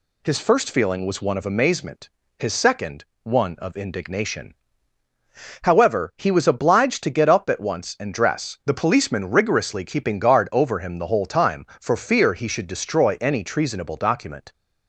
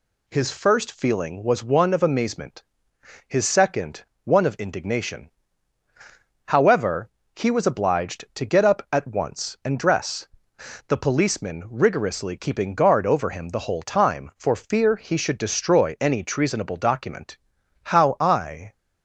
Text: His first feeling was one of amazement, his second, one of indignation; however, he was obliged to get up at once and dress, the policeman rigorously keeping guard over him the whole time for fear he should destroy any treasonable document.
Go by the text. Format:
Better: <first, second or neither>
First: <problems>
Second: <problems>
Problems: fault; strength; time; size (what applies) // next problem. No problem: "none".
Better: first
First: none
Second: goes on to say "How I"; noticeable; from 17.8 s on; 0.88 s long